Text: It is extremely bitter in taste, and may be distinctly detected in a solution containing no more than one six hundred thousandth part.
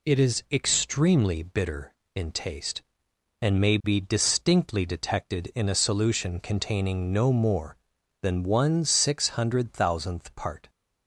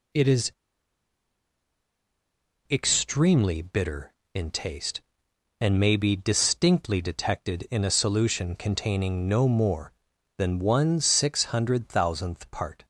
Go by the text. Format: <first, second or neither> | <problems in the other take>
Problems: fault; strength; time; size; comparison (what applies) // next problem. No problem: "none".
first | pauses between "is" and "extremely"; strong; at 0.5 s; 2.1 s long